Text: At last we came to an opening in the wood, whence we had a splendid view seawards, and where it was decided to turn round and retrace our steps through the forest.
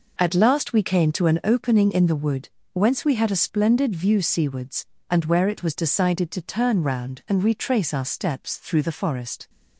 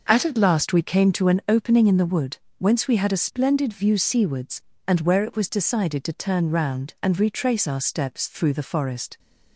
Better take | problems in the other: first | says "At" twice; at 0.2 s

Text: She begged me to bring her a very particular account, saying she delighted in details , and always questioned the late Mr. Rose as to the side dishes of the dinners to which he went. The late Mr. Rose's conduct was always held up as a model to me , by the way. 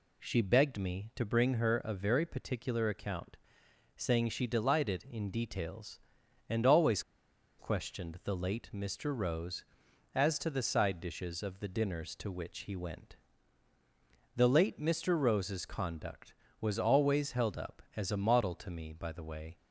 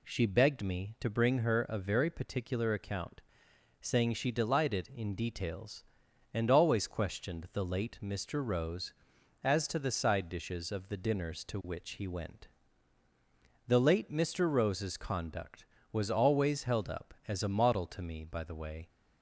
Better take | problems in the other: second | pauses between "always" and "questioned"; noticeable; at 7.0 s; 0.57 s long

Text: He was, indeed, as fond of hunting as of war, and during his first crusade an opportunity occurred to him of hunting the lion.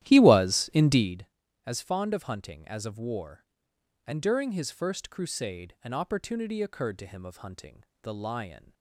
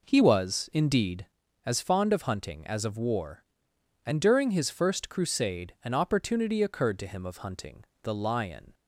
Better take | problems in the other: second | starts louder than the rest; strong; until 1.2 s; 13 dB // pauses between "hunting" and "the"; slight; at 7.8 s; 0.18 s long; slight in the second

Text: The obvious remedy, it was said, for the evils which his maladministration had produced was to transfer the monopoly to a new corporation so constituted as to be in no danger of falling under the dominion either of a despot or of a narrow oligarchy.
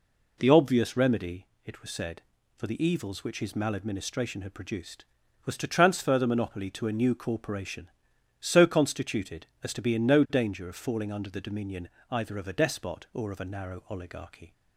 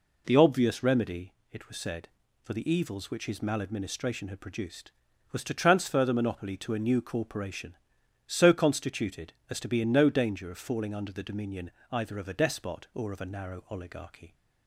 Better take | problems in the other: neither | pauses between "dominion" and "either"; slight; the same in both

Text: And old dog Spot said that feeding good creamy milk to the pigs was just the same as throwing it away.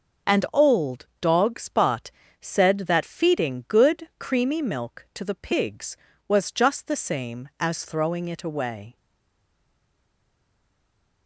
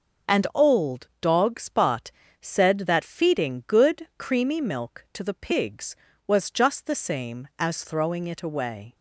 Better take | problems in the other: second | starts louder than the rest; until 1.4 s; 6.5 dB; also in the second // pauses between "Spot" and "said"; slight; at 2.0 s; 0.30 s long; slight in the second // stays silent after the last word; from 8.9 s on; 2.3 s long

